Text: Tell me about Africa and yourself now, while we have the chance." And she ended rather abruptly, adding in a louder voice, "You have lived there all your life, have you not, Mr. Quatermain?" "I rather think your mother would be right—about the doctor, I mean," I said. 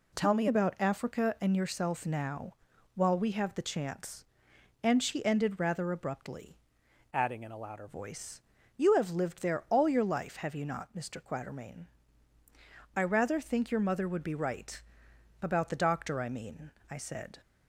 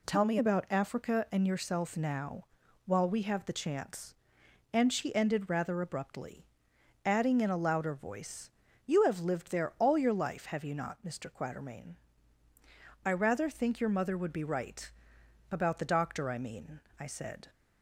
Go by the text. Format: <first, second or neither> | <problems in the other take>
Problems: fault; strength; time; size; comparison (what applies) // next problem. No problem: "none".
second | changes voice from "adding" to "louder"; from 7.1 to 7.8 s; 0.7 s long